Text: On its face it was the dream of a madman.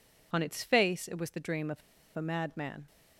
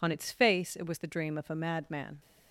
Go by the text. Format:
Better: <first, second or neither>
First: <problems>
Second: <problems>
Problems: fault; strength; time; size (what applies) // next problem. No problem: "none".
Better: second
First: pauses between "of" and "a"; slight; at 1.8 s; 0.35 s long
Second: none